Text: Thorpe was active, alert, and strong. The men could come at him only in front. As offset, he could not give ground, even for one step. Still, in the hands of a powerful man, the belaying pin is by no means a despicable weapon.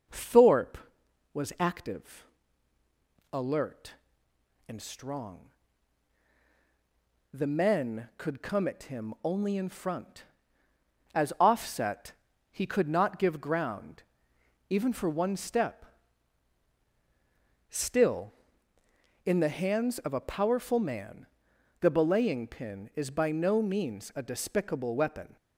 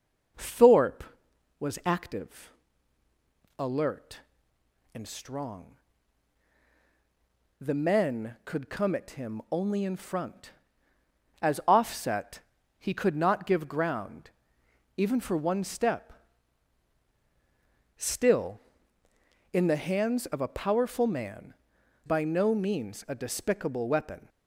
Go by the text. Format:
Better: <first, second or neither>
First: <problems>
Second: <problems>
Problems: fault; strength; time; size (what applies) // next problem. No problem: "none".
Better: first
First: none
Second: skips "the belaying pin is"; at 21.7 s